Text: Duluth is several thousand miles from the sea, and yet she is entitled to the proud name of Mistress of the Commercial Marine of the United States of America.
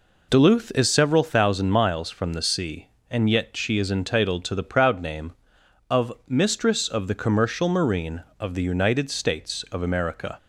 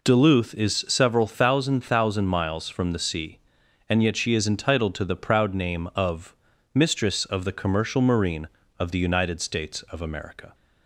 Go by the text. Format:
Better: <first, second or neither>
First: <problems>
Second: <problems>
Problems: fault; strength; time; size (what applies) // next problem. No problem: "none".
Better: first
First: none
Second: says "thousand" twice; at 1.8 s // pauses between "of" and "Mistress"; at 6.3 s; 0.38 s long